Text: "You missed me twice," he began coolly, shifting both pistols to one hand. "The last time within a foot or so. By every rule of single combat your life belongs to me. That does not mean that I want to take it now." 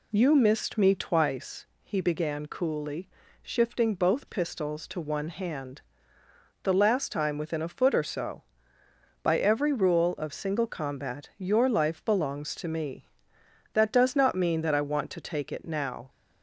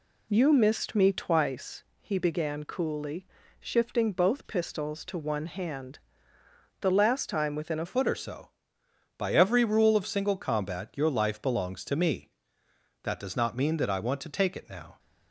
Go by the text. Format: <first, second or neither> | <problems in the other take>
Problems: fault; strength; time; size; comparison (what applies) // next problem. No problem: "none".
first | changes voice at "foot"; from 7.8 s on; 7.1 s long